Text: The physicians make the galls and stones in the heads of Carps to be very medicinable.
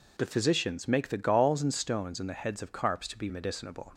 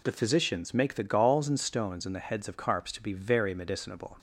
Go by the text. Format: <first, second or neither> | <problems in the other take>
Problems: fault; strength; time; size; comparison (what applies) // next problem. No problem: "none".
second | skips "very"; at 3.2 s